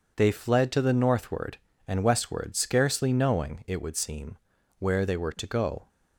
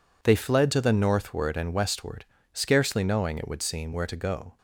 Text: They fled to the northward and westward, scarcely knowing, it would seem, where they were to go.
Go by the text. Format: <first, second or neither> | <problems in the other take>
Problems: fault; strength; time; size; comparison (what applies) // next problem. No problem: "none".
first | skips "they were"; at 4.0 s